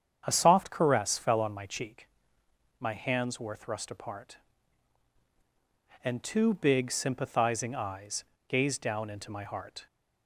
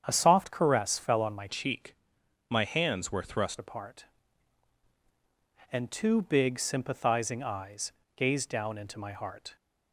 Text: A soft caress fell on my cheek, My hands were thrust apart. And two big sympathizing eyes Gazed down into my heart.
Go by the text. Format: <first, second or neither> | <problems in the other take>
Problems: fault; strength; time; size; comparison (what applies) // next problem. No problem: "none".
first | starts louder than the rest; strong; until 1.0 s; 8 dB; strong in the first // changes voice from "cheek" to "thrust"; from 1.4 to 3.5 s; 2.1 s long // pauses between "eyes" and "Gazed"; slight; at 7.9 s; 0.24 s long; slight in the first